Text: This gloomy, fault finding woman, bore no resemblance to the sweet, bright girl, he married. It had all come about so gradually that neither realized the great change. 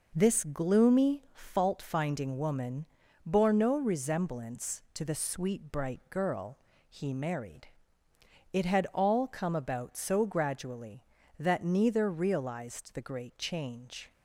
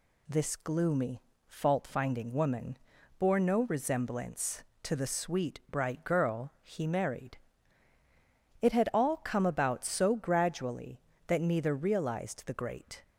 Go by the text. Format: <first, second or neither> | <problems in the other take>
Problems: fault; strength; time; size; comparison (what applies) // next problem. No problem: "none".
first | stops before "change"; at 13.0 s